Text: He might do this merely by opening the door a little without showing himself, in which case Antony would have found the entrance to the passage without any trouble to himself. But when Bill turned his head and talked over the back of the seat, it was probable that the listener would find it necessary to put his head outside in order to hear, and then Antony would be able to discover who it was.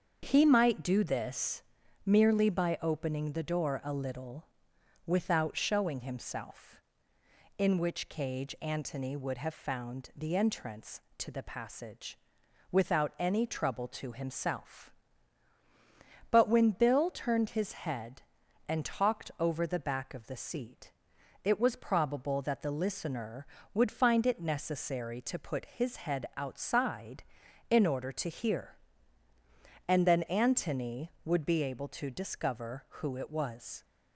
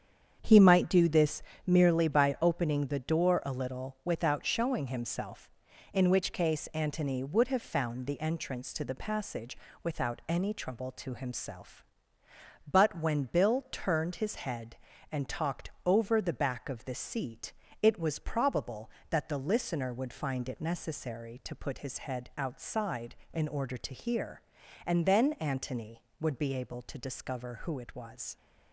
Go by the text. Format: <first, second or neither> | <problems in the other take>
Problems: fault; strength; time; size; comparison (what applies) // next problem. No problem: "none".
second | starts louder than the rest; until 1.2 s; 7 dB; strong in the second // pauses between "this" and "merely"; at 1.6 s; 0.44 s long; slight in the second // pauses between "little" and "without"; noticeable; at 4.4 s; 0.60 s long // says "cage" for "case"; at 8.0 s // pauses between "passage" and "without"; noticeable; at 12.1 s; 0.54 s long; slight in the second